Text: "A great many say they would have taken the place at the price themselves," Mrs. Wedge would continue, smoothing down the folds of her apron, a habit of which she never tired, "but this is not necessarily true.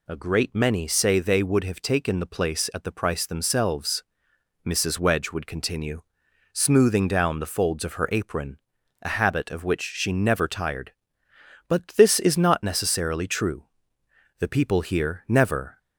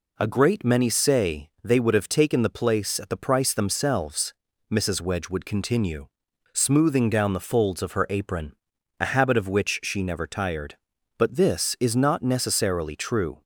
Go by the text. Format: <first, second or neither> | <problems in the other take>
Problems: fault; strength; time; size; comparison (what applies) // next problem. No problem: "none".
second | goes on to say "The people here never"; from 14.3 s on; 1.4 s long